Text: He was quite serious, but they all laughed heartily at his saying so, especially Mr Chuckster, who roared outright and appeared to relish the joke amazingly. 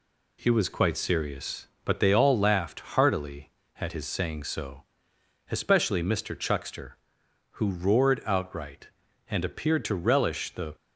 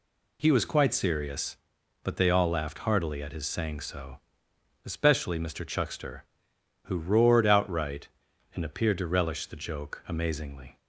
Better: second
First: stops before "joke amazingly"; at 10.7 s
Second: none

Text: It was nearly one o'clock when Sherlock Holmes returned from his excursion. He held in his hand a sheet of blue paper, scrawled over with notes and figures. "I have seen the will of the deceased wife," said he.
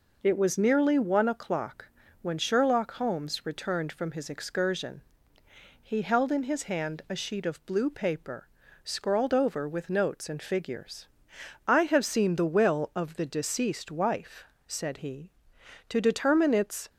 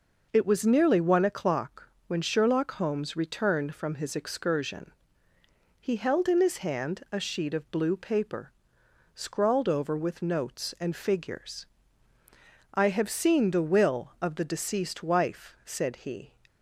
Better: second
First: pauses between "o'clock" and "when"; slight; at 1.8 s; 0.34 s long // goes on to say "To determine its"; noticeable; from 15.8 s on; 1.0 s long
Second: pauses between "o'clock" and "when"; slight; at 1.8 s; 0.18 s long

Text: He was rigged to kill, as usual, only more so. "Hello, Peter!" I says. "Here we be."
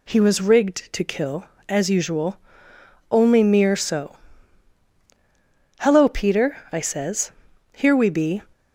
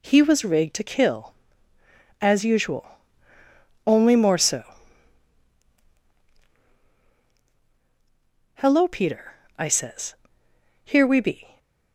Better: second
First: says "mere" for "more"; at 3.4 s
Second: none

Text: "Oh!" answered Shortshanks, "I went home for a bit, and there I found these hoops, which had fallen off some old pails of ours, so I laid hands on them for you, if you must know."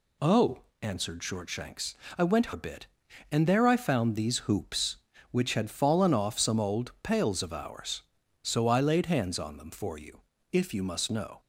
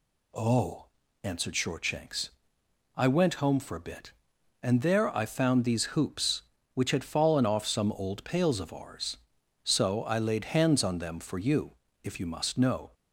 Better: second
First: skips "home for"; at 2.5 s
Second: none

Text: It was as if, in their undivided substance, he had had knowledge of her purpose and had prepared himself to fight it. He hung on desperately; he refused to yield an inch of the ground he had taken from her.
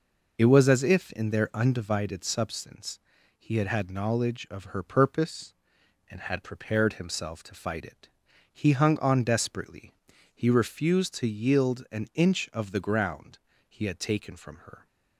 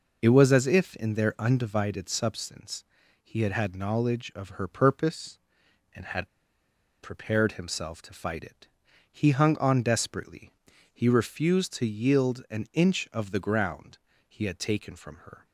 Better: first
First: pauses between "ground" and "he"; slight; at 13.3 s; 0.30 s long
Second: pauses between "had" and "prepared"; noticeable; at 6.2 s; 0.74 s long // pauses between "ground" and "he"; slight; at 13.9 s; 0.30 s long

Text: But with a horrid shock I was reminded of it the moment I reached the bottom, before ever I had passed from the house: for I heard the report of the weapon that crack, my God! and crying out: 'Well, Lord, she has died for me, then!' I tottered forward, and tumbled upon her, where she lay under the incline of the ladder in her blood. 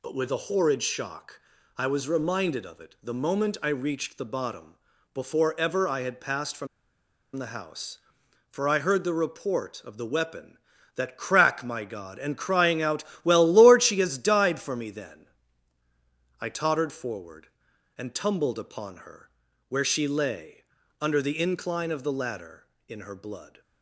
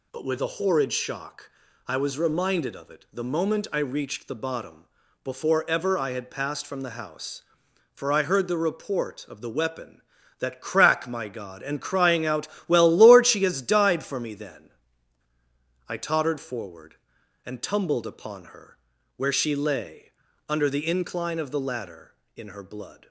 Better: second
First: pauses between "shock" and "I"; slight; at 1.4 s; 0.36 s long // pauses between "from" and "the"; noticeable; at 6.6 s; 0.69 s long // pauses between "lay" and "under"; slight; at 20.6 s; 0.36 s long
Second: pauses between "shock" and "I"; slight; at 1.5 s; 0.36 s long // pauses between "lay" and "under"; slight; at 20.1 s; 0.36 s long

